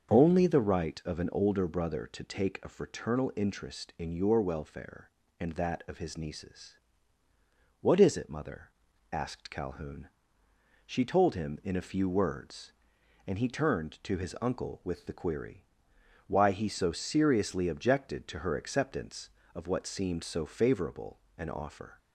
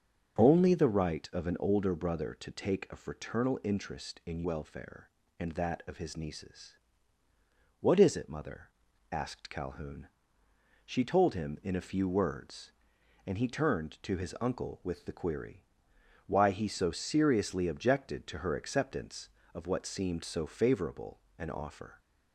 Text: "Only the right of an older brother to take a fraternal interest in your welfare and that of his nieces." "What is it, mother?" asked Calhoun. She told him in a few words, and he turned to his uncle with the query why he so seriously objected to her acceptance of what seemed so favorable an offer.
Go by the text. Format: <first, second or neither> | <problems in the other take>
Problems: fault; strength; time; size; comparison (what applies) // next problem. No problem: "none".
first | starts louder than the rest; strong; until 1.4 s; 7.5 dB; also in the first // skips "your"; at 4.4 s // pauses between "query" and "why"; noticeable; at 15.6 s; 0.62 s long; noticeable in the first // pauses between "favorable" and "an"; slight; at 21.2 s; 0.16 s long; slight in the first